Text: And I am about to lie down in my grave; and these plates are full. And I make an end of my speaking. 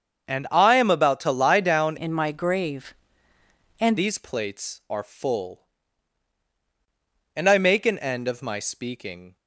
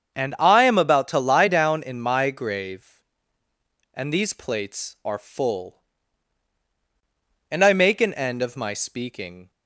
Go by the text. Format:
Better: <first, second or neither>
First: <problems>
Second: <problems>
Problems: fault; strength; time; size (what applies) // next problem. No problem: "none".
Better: second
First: starts louder than the rest; until 1.3 s; 7 dB // changes voice from "in" to "and"; from 1.9 to 3.9 s; 2.0 s long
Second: starts louder than the rest; strong; until 1.2 s; 7 dB